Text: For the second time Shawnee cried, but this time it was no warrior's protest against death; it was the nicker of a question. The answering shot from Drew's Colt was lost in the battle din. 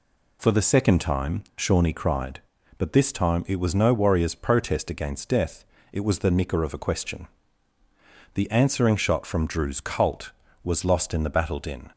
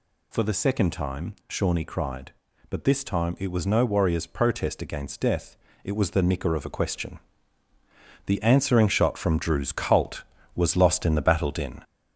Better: first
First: pauses between "time" and "Shawnee"; slight; at 1.4 s; 0.16 s long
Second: gets louder; noticeable; throughout; 4 dB // pauses between "time" and "Shawnee"; slight; at 1.3 s; 0.16 s long

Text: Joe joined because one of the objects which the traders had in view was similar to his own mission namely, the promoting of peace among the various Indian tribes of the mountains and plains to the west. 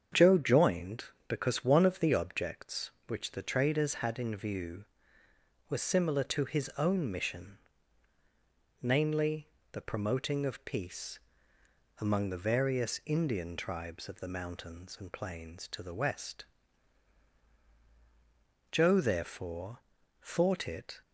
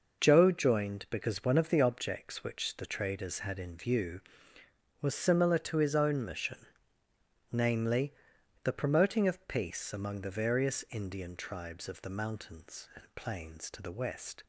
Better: second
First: starts louder than the rest; strong; until 1.3 s; 7.5 dB // pauses between "mission" and "namely"; strong; at 7.5 s; 1.2 s long // pauses between "peace" and "among"; noticeable; at 11.1 s; 0.82 s long // goes on to say "Joe therefore thought it"; strong; from 18.7 s on; 2.3 s long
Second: pauses between "mission" and "namely"; noticeable; at 6.5 s; 0.94 s long

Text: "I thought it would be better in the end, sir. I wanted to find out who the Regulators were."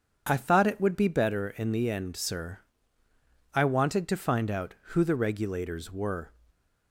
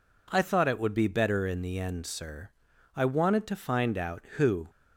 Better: first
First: none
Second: stops before "the Regulators were"; at 4.6 s

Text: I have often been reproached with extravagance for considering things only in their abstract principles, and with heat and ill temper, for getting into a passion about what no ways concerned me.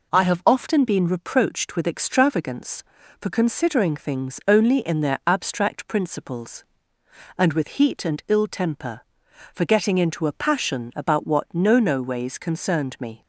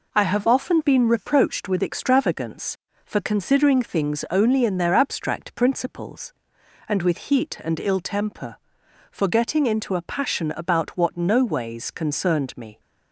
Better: second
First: says "no" twice; at 11.7 s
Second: none

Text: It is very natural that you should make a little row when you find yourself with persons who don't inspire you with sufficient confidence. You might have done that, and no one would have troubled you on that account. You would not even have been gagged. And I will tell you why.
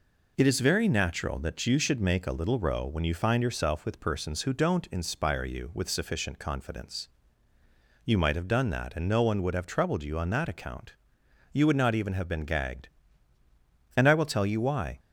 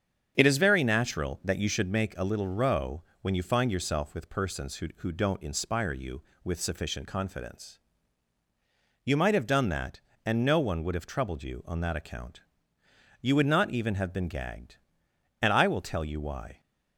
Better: first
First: none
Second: starts louder than the rest; strong; until 1.3 s; 7.5 dB // pauses between "row" and "when"; slight; at 3.0 s; 0.20 s long // says "who" twice; at 4.9 s

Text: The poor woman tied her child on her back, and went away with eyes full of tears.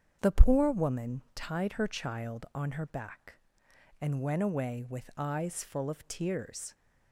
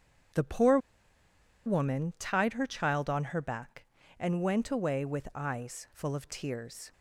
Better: first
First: starts louder than the rest; until 1.2 s; 6 dB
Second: starts louder than the rest; strong; until 2.2 s; 8 dB // pauses between "poor" and "woman"; noticeable; at 0.7 s; 0.87 s long

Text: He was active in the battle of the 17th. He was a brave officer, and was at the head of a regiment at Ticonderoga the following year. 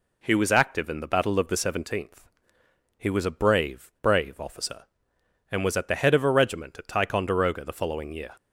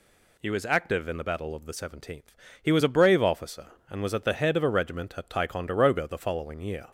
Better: second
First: says "brave" twice; at 4.0 s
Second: none

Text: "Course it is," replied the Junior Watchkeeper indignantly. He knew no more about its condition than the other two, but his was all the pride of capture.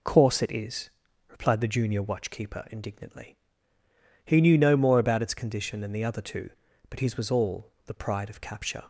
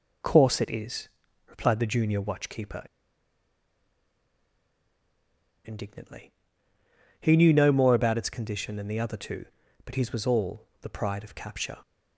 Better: first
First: none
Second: pauses between "Watchkeeper" and "indignantly"; strong; at 2.8 s; 2.8 s long

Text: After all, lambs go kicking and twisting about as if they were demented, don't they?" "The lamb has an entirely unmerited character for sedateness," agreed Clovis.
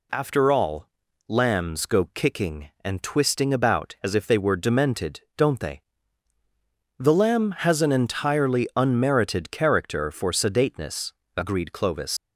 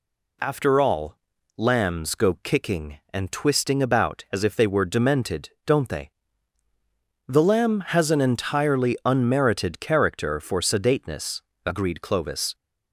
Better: second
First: leaves "Clovis" unfinished; at 12.1 s; 85 ms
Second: none

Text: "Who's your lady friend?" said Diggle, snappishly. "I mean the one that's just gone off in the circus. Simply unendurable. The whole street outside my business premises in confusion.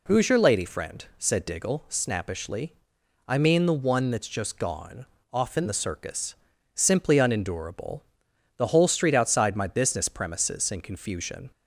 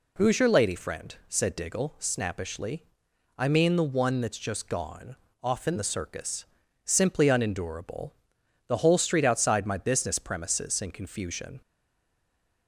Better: first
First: pauses between "gone" and "off"; slight; at 5.0 s; 0.28 s long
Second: pauses between "gone" and "off"; slight; at 5.1 s; 0.28 s long // stays silent after the last word; from 11.6 s on; 1.0 s long

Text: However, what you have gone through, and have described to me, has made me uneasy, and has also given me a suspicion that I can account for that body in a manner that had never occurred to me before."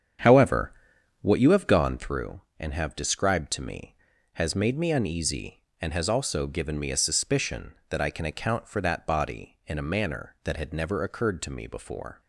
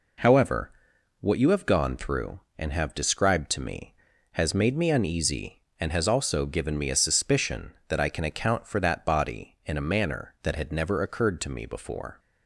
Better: second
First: starts louder than the rest; strong; until 2.0 s; 8 dB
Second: none

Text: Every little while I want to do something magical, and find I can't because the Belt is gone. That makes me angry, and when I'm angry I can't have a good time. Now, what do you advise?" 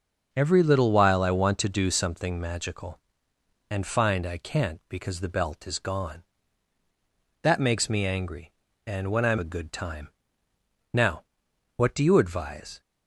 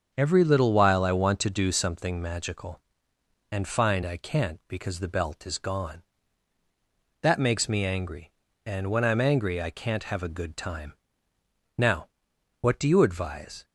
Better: second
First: starts louder than the rest; until 1.3 s; 6.5 dB // skips "angry I can't have"; at 9.3 s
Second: starts louder than the rest; until 1.1 s; 7 dB

